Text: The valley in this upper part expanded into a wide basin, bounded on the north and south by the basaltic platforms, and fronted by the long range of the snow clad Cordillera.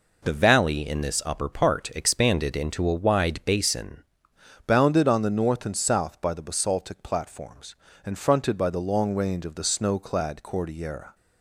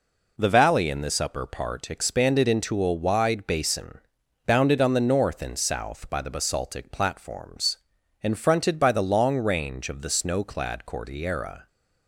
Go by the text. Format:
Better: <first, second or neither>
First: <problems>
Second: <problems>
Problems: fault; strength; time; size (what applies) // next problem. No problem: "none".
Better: second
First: changes voice at "bounded"; from 4.6 s on; 6.5 s long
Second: none